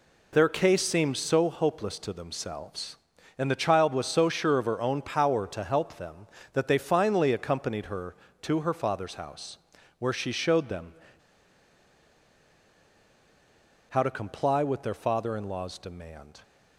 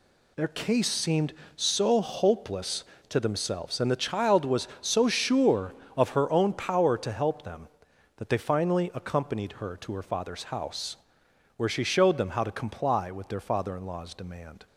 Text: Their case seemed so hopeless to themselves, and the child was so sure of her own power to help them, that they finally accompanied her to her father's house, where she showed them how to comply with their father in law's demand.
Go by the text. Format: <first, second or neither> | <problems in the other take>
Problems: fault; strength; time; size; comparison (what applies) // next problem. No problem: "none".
second | pauses between "them" and "how"; strong; at 10.9 s; 2.9 s long